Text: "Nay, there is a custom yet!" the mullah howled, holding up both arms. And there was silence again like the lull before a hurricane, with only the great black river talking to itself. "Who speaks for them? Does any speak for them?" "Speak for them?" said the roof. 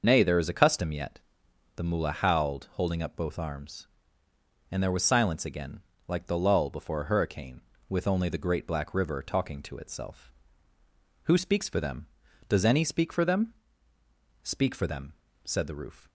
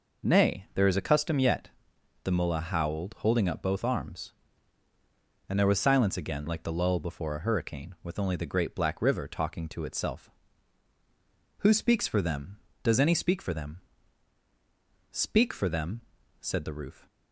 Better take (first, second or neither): second